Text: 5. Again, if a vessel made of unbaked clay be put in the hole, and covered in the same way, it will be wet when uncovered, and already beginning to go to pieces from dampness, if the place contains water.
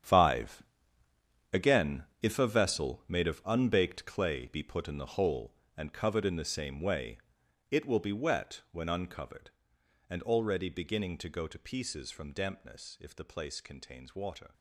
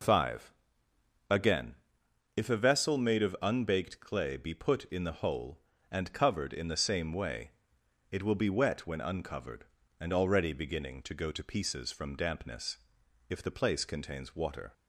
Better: second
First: gets quieter; strong; throughout; 13 dB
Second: none

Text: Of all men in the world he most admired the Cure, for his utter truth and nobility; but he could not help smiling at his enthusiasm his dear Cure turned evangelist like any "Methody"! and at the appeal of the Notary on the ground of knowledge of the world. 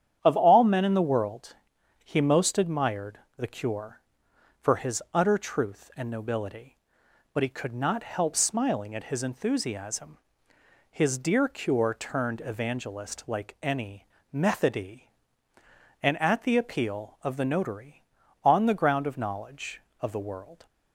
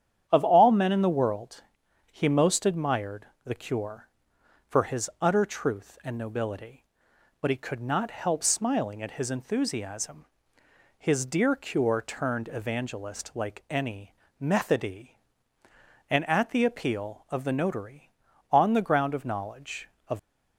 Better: first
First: starts louder than the rest; strong; until 1.2 s; 9.5 dB // pauses between "world" and "he"; noticeable; at 1.5 s; 0.48 s long // pauses between "admired" and "the"; slight; at 3.1 s; 0.18 s long // pauses between "enthusiasm" and "his"; noticeable; at 10.1 s; 0.74 s long // pauses between "any" and "Methody"; slight; at 14.0 s; 0.22 s long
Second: starts louder than the rest; strong; until 1.2 s; 9.5 dB // pauses between "world" and "he"; noticeable; at 1.6 s; 0.48 s long // pauses between "admired" and "the"; slight; at 3.2 s; 0.18 s long // pauses between "enthusiasm" and "his"; noticeable; at 10.2 s; 0.74 s long // pauses between "any" and "Methody"; slight; at 14.1 s; 0.22 s long // stops before "the world"; at 20.1 s

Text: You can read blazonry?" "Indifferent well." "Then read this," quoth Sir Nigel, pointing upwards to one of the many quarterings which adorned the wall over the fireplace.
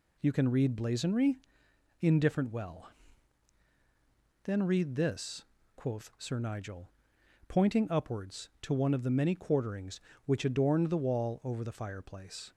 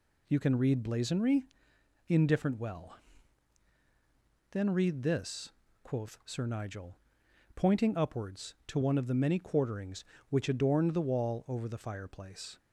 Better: neither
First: none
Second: none

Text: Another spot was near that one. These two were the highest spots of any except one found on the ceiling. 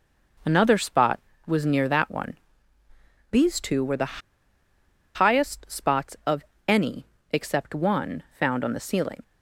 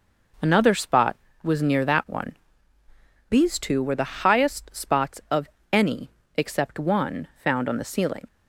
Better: second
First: pauses between "the" and "highest"; noticeable; at 4.2 s; 0.95 s long // pauses between "of" and "any"; slight; at 6.4 s; 0.24 s long // pauses between "any" and "except"; slight; at 7.0 s; 0.26 s long // pauses between "one" and "found"; slight; at 8.2 s; 0.16 s long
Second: pauses between "of" and "any"; slight; at 5.4 s; 0.24 s long // pauses between "any" and "except"; slight; at 6.1 s; 0.26 s long // pauses between "one" and "found"; slight; at 7.2 s; 0.16 s long

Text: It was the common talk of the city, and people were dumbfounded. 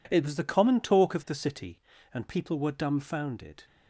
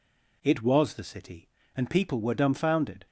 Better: first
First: none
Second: skips "the common talk of"; at 0.9 s

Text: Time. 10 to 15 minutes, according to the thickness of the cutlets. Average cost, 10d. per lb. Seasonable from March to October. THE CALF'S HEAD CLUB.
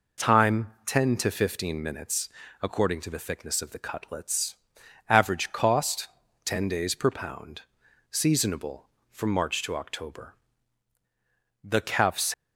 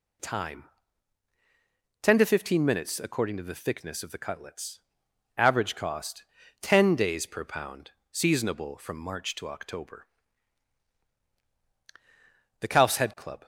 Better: second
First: stops before "HEAD CLUB"; at 12.3 s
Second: none

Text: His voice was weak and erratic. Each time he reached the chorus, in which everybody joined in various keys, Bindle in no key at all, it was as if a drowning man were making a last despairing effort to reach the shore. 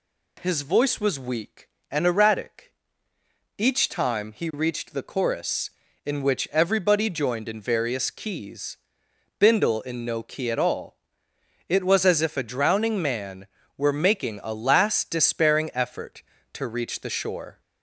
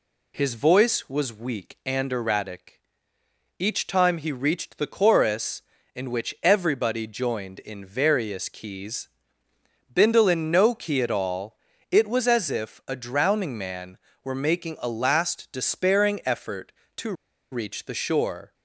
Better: first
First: none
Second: pauses between "to" and "reach"; at 17.1 s; 0.38 s long

